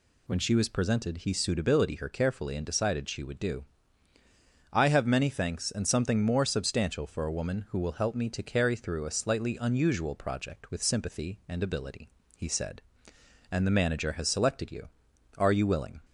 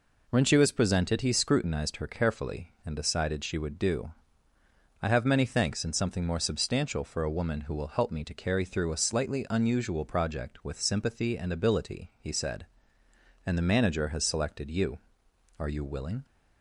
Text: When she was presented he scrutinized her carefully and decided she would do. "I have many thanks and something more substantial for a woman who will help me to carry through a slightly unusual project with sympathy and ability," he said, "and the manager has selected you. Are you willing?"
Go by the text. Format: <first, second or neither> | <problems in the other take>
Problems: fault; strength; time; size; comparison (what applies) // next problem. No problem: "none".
second | says "suitability" for "scrutinized"; at 1.3 s